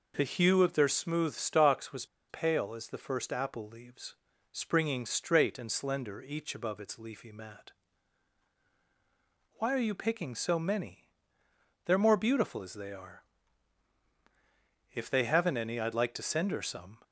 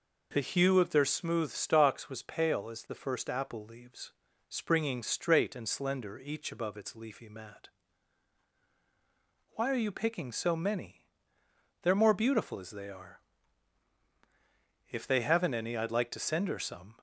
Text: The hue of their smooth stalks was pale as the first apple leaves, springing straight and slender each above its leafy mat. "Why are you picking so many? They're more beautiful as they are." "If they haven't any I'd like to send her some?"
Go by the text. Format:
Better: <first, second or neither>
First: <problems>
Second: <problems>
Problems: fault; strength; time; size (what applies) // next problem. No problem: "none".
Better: second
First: pauses between "was" and "pale"; slight; at 2.0 s; 0.24 s long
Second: none